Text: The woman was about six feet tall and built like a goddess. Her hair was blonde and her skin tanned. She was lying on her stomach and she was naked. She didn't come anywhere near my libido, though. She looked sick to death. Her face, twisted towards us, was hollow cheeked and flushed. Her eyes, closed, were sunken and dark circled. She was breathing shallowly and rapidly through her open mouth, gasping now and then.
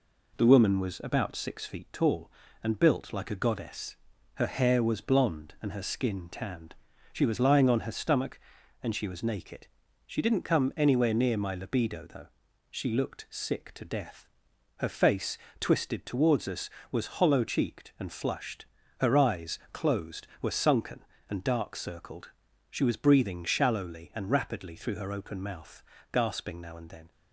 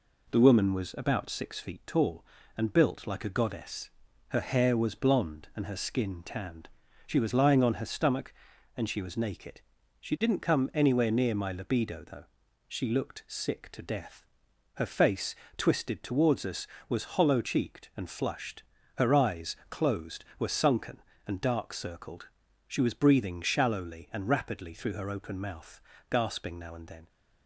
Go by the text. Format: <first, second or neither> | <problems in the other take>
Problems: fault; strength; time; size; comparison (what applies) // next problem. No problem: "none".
neither | none